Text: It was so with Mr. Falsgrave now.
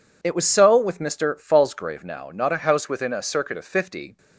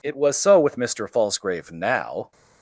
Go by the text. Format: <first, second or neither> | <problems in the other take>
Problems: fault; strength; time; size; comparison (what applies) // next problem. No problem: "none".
second | goes on to say "Not a house within a circuit of fifty"; strong; from 2.3 s on; 1.8 s long